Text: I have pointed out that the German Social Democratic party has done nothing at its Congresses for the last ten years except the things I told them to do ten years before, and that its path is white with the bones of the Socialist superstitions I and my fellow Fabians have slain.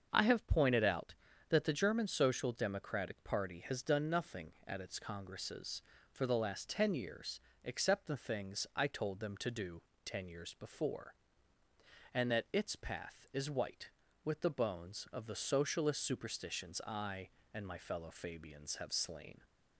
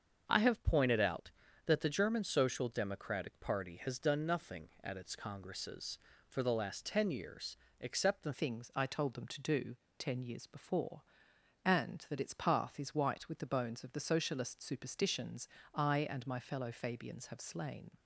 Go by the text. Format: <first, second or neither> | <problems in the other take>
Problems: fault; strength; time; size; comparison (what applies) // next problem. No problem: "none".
first | starts louder than the rest; until 1.2 s; 7 dB; also in the first // pauses between "years" and "except"; slight; at 7.5 s; 0.24 s long; slight in the first // changes voice at "things"; from 8.3 s on; 9.6 s long // pauses between "do" and "ten"; slight; at 9.7 s; 0.22 s long; slight in the first // pauses between "superstitions" and "I"; slight; at 15.4 s; 0.26 s long